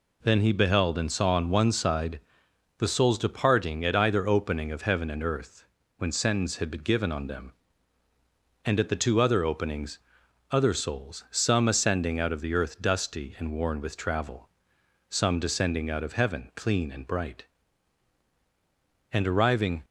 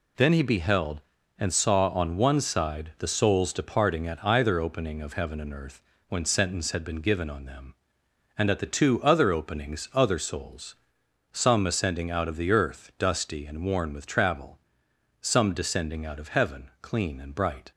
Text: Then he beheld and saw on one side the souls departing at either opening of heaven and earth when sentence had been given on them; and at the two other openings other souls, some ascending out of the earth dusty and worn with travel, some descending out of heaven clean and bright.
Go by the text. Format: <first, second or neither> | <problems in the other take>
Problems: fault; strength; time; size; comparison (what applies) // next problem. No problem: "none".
second | pauses between "side" and "the"; noticeable; at 2.1 s; 0.58 s long // pauses between "earth" and "when"; slight; at 5.6 s; 0.32 s long; slight in the second // pauses between "openings" and "other"; noticeable; at 9.9 s; 0.54 s long // goes on to say "And arriving"; noticeable; from 19.1 s on; 0.72 s long